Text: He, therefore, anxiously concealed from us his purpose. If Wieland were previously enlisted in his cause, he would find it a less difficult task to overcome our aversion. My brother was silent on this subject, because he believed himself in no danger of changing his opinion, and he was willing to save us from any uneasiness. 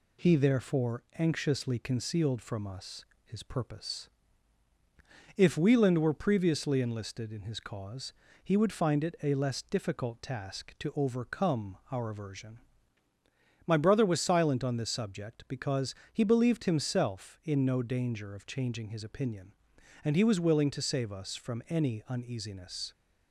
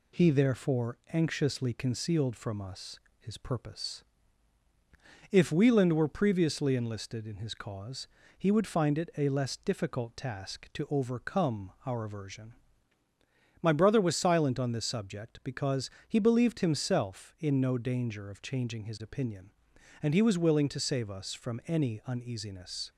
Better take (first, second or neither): neither